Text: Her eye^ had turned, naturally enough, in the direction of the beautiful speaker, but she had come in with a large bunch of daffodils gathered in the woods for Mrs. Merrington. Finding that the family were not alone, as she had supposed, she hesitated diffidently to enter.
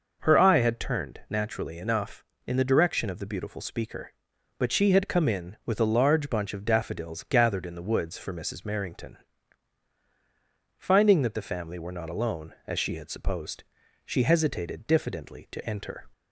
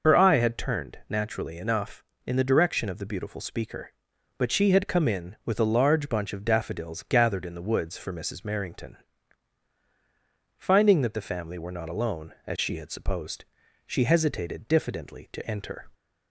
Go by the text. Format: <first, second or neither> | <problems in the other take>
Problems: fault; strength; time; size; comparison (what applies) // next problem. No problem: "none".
first | loses the start of "Her"; at 0.0 s; 55 ms